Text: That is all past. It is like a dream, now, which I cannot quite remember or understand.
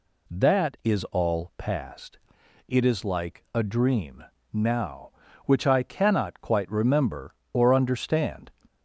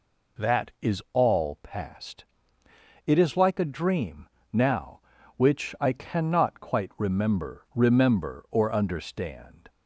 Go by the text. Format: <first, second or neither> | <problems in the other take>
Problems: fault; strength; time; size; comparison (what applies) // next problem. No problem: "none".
first | says "remember" twice; at 7.7 s